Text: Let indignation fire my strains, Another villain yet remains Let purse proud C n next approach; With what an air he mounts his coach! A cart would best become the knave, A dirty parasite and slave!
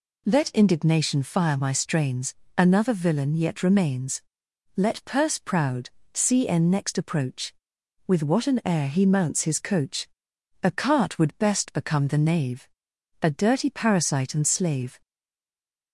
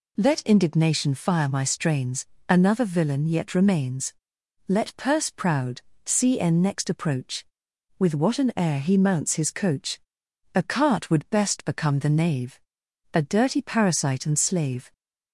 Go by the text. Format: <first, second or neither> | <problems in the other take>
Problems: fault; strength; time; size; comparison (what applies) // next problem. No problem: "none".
second | pauses between "remains" and "Let"; noticeable; at 4.2 s; 0.56 s long; noticeable in the second // pauses between "proud" and "C"; slight; at 5.8 s; 0.24 s long; slight in the second // stays silent after the last word; slight; from 15.0 s on; 0.9 s long